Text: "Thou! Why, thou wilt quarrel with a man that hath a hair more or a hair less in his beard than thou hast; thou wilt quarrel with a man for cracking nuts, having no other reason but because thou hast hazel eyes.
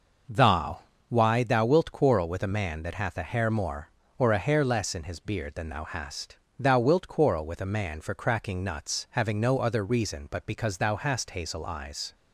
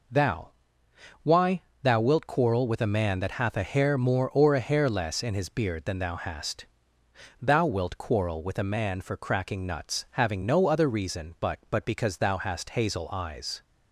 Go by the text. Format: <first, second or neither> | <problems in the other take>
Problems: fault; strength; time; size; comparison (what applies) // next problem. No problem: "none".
first | says "but" twice; at 11.7 s